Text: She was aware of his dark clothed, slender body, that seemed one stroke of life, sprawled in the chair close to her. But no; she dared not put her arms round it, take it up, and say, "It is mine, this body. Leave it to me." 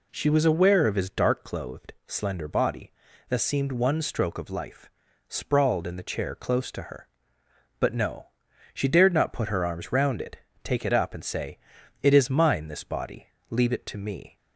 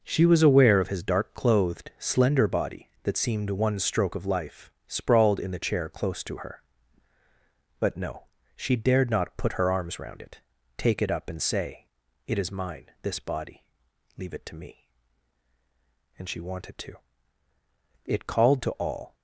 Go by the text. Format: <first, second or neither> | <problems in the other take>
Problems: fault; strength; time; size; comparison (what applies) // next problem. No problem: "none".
first | goes on to say "And she wanted to It called to all"; strong; from 16.1 s on; 2.9 s long